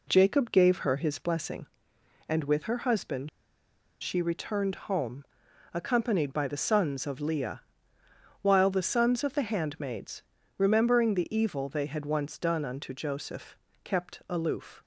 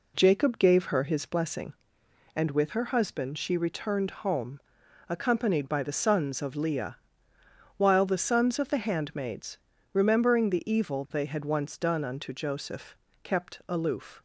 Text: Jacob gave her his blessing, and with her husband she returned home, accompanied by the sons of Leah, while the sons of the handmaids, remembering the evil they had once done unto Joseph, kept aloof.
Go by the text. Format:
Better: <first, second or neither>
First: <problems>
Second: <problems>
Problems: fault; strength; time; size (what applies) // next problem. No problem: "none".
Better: second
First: pauses between "husband" and "she"; noticeable; at 3.2 s; 0.72 s long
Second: none